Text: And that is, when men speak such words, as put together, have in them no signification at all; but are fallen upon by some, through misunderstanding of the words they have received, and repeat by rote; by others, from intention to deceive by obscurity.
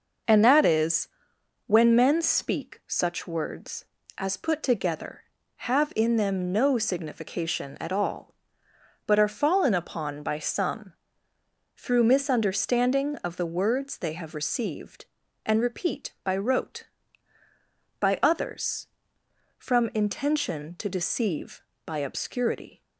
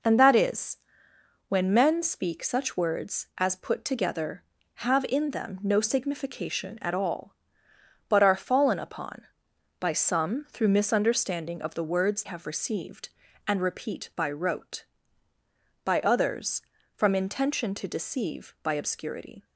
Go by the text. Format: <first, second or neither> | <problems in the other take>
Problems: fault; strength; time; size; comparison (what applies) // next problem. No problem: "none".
first | skips "they"; at 12.2 s